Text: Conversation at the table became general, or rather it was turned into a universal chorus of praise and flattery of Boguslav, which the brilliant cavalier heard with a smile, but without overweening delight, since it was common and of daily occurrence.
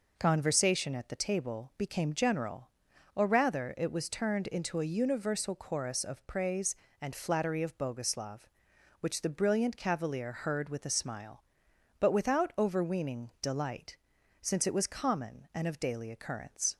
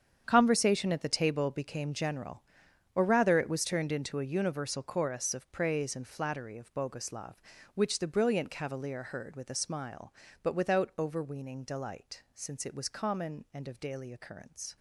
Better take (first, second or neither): first